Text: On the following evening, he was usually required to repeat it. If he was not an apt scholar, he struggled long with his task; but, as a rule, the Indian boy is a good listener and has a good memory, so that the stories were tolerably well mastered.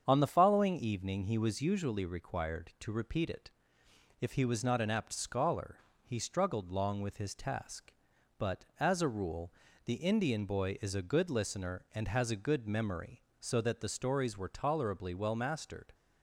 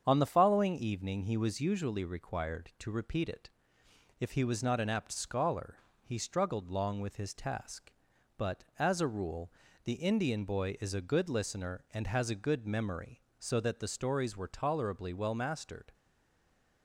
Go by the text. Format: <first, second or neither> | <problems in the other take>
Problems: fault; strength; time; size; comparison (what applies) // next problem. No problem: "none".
first | starts louder than the rest; strong; until 1.0 s; 7.5 dB; strong in the first // stays silent after the last word; slight; from 15.9 s on; 0.9 s long